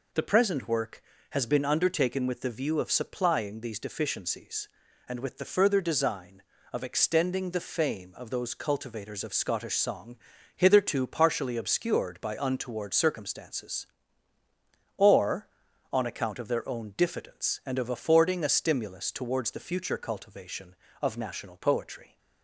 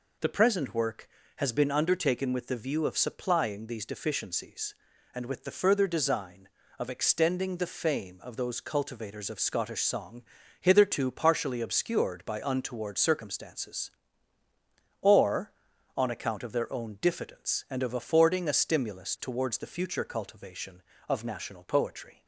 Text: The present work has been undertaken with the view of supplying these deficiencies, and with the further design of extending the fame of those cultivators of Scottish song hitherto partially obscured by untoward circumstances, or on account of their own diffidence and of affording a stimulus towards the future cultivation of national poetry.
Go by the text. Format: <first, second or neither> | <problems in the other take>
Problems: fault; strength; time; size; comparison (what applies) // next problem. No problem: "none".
neither | pauses between "song" and "hitherto"; the same in both